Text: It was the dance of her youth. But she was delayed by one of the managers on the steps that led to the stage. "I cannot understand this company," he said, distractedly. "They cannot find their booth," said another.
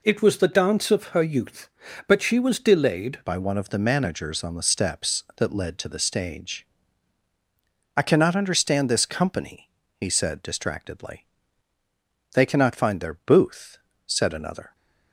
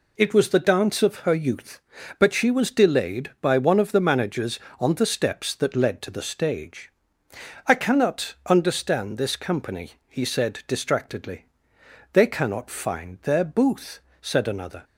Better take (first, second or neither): second